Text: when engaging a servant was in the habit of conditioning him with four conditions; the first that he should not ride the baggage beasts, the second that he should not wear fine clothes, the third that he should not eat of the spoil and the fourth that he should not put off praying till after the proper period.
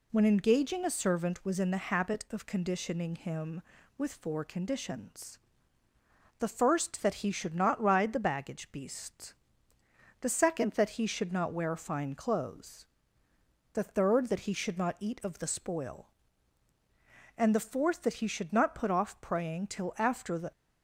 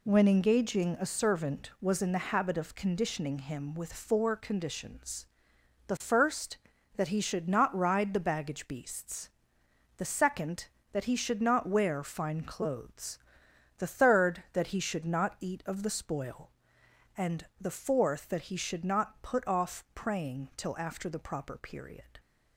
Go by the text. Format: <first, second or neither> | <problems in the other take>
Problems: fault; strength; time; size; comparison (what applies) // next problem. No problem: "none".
second | stops before "proper period"; at 20.5 s